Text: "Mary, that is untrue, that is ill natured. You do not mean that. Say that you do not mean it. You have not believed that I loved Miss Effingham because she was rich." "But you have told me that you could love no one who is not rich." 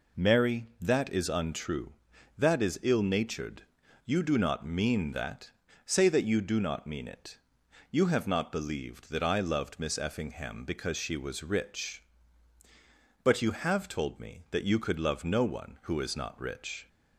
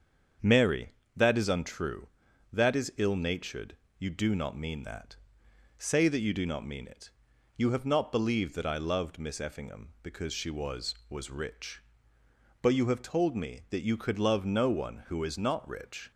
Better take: first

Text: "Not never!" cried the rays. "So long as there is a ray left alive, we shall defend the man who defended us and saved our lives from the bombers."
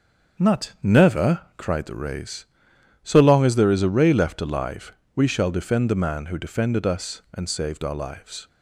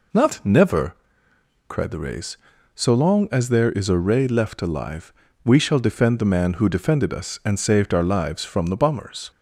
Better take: second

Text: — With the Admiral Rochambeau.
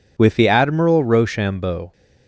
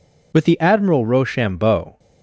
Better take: neither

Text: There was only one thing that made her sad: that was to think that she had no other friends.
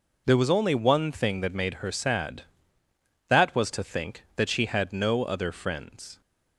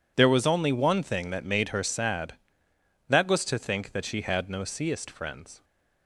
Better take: first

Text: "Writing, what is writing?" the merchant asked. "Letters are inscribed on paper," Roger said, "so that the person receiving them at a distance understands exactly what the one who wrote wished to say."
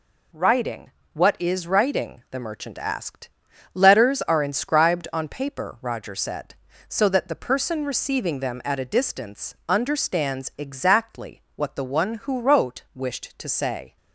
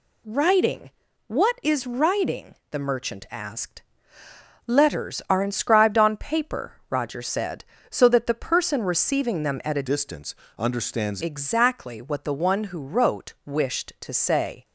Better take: first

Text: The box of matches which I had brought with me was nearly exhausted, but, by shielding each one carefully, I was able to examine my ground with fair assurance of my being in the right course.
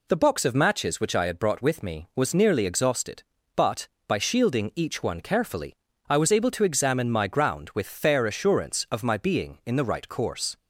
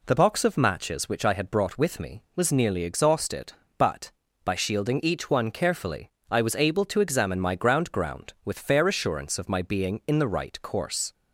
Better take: first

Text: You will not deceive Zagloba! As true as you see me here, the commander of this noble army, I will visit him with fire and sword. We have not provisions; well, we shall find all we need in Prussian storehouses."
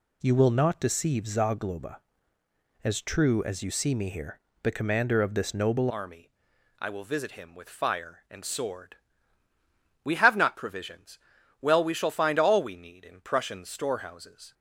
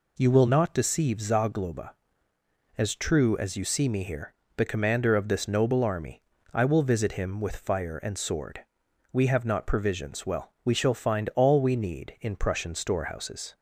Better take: second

